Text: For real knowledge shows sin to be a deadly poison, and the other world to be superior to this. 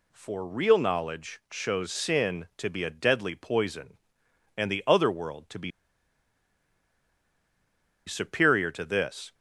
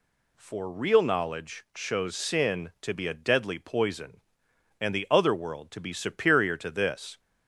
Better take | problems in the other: second | pauses between "be" and "superior"; strong; at 5.7 s; 2.3 s long

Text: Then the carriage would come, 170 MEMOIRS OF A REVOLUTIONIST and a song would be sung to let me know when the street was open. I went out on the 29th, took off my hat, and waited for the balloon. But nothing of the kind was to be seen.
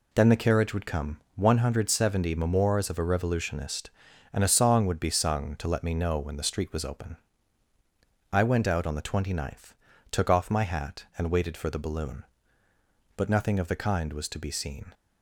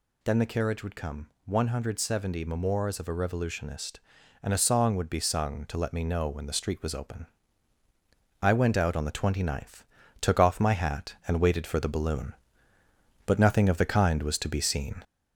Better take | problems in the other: first | gets louder; noticeable; throughout; 4 dB

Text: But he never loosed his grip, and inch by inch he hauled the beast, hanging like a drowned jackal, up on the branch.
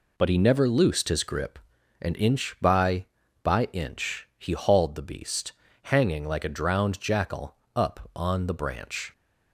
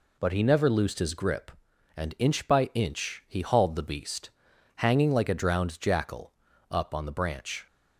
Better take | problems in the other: second | says "by" twice; at 3.4 s

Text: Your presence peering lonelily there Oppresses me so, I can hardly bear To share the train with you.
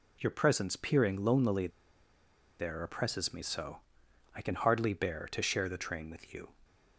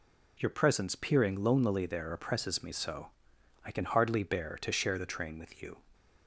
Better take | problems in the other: second | pauses between "lonelily" and "there"; noticeable; at 1.7 s; 0.89 s long

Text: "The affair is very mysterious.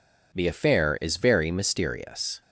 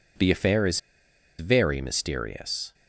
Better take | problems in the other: first | pauses between "is" and "very"; noticeable; at 0.7 s; 0.59 s long

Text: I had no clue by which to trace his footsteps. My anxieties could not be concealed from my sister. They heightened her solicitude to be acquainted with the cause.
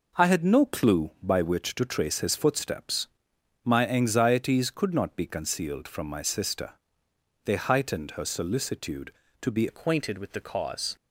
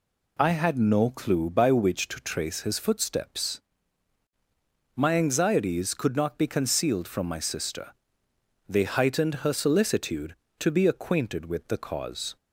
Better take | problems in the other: second | changes voice at "acquainted"; from 9.6 s on; 1.3 s long

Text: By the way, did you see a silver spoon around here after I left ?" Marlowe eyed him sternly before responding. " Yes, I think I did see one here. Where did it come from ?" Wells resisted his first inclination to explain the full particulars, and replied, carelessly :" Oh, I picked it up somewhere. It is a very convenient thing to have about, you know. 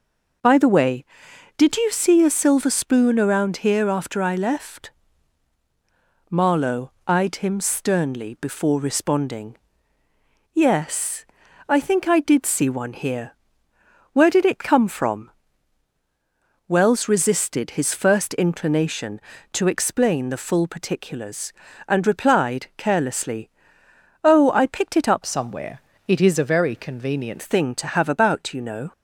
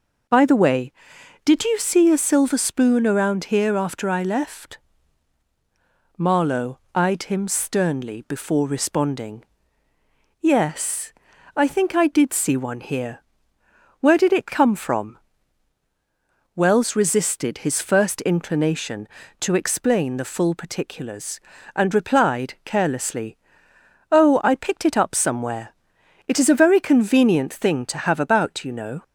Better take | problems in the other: second | starts louder than the rest; until 1.9 s; 6.5 dB; also in the second // pauses between "Marlowe" and "eyed"; slight; at 6.9 s; 0.16 s long; slight in the second // changes voice from "somewhere" to "convenient"; from 25.2 to 27.3 s; 2.1 s long

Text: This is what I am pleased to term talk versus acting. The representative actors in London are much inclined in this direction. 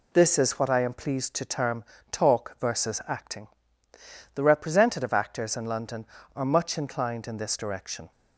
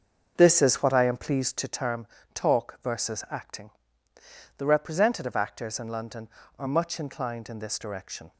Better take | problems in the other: first | starts louder than the rest; until 1.8 s; 6.5 dB // pauses between "term" and "talk"; slight; at 2.0 s; 0.28 s long; slight in the first

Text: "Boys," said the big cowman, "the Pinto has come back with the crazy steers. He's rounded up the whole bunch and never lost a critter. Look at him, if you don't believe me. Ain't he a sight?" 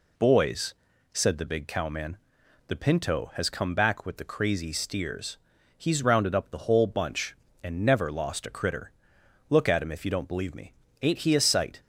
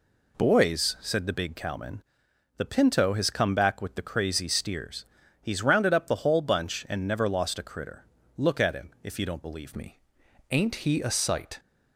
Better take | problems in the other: first | changes voice at "me"; from 9.7 s on; 1.8 s long

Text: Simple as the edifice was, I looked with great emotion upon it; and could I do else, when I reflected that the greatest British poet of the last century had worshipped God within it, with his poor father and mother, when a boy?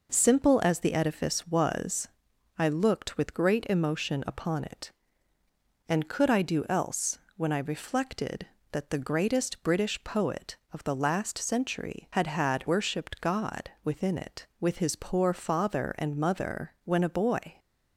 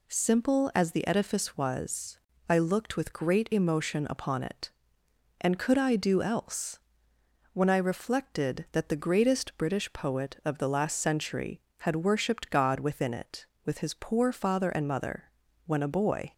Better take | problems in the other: second | says "had" twice; at 12.2 s // pauses between "God" and "within"; slight; at 13.6 s; 0.16 s long

